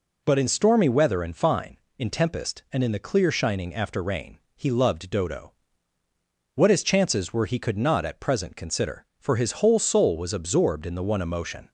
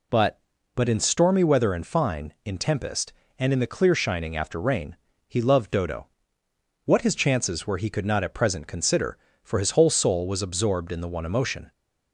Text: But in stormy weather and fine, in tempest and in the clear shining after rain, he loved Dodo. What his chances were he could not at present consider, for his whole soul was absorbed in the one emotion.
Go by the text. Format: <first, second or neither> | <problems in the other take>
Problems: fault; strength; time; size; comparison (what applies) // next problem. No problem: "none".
first | says "But" twice; at 0.7 s